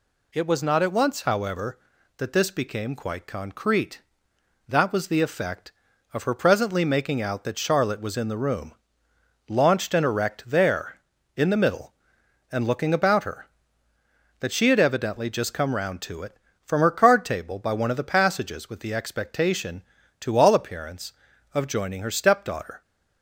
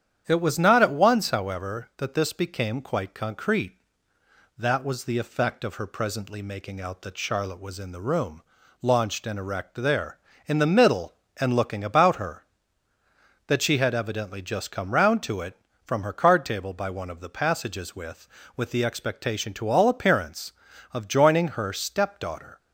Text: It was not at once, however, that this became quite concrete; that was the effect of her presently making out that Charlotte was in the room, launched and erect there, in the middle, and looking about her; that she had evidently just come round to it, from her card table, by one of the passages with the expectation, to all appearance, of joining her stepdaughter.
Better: first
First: none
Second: starts louder than the rest; strong; until 1.2 s; 9.5 dB // says "with" twice; at 18.5 s

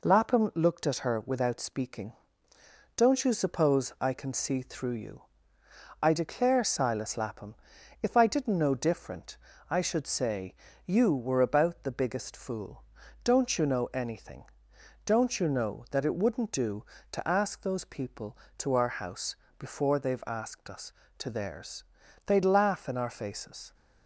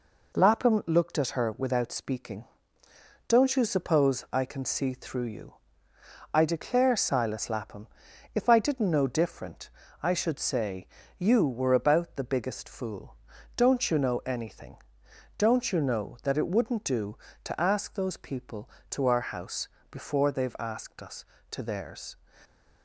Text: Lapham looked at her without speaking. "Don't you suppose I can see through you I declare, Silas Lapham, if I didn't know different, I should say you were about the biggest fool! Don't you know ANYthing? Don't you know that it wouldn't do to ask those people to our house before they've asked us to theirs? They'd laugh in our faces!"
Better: first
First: pauses between "you" and "I"; noticeable; at 5.2 s; 0.78 s long // pauses between "say" and "you"; slight; at 10.5 s; 0.32 s long // pauses between "house" and "before"; slight; at 19.3 s; 0.22 s long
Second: pauses between "you" and "I"; noticeable; at 5.5 s; 0.78 s long // pauses between "say" and "you"; slight; at 10.8 s; 0.32 s long // pauses between "house" and "before"; slight; at 19.6 s; 0.22 s long // stops before "They'd laugh in our faces"; at 22.4 s

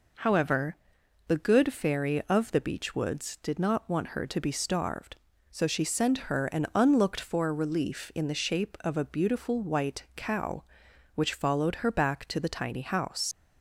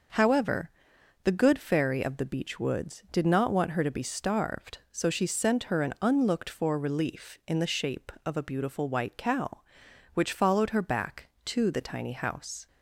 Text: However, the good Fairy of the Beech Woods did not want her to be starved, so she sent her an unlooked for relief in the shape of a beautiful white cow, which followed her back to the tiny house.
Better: second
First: leaves "house" unfinished; at 13.3 s; 95 ms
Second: none

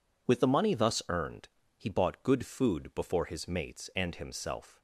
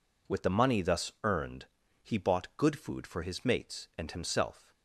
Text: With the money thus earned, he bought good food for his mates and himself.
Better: second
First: says "before" for "for"; at 2.9 s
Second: none

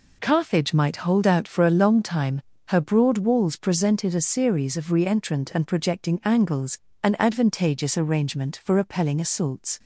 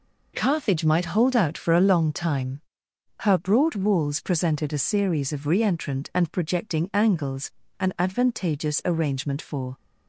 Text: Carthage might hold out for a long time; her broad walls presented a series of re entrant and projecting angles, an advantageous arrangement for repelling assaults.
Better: first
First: none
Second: stops before "repelling assaults"; at 9.7 s

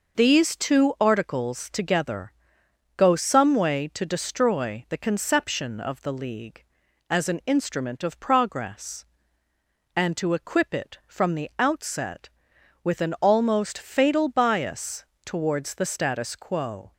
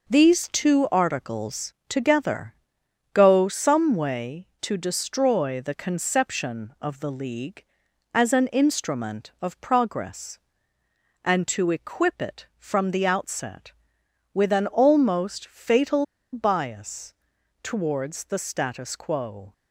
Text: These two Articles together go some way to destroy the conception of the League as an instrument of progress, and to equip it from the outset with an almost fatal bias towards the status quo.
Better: first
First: pauses between "together" and "go"; noticeable; at 2.3 s; 0.64 s long // pauses between "bias" and "towards"; slight; at 15.0 s; 0.20 s long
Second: pauses between "Articles" and "together"; slight; at 1.7 s; 0.16 s long // pauses between "together" and "go"; noticeable; at 2.5 s; 0.62 s long // pauses between "fatal" and "bias"; slight; at 16.0 s; 0.28 s long // pauses between "bias" and "towards"; noticeable; at 17.1 s; 0.50 s long

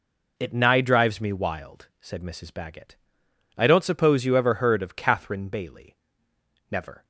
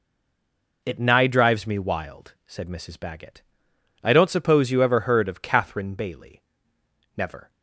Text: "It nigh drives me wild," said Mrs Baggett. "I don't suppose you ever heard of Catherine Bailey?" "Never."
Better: first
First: none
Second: stays silent before the first word; slight; until 0.8 s; 0.8 s long

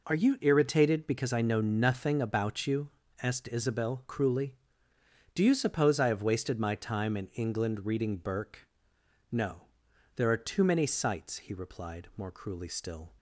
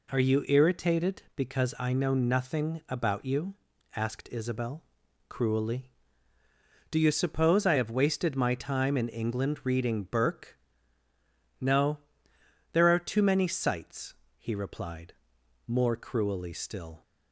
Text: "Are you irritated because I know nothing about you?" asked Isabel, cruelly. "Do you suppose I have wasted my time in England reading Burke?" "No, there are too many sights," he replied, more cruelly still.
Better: neither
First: none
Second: none

